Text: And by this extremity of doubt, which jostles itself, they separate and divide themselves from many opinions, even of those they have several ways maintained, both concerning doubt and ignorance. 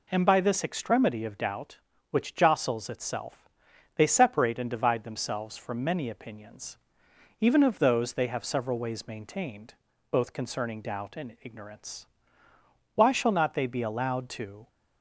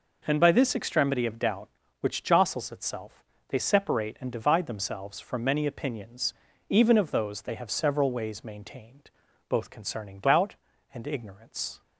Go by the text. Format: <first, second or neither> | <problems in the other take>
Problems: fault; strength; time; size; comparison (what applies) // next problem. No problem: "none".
second | goes on to say "Why shall not they be allowed to"; strong; from 12.9 s on; 1.7 s long